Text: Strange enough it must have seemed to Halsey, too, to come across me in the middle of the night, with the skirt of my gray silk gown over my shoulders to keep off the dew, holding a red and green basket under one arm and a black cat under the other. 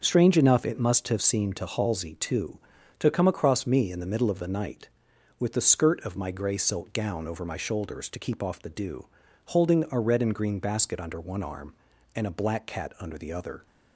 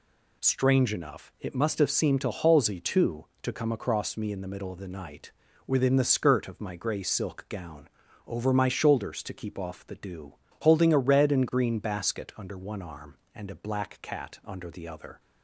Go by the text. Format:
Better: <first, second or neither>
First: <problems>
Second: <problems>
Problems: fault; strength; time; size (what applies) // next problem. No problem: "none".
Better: first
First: none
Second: says "within" for "with"; at 5.6 s // pauses between "gown" and "over"; at 7.8 s; 0.40 s long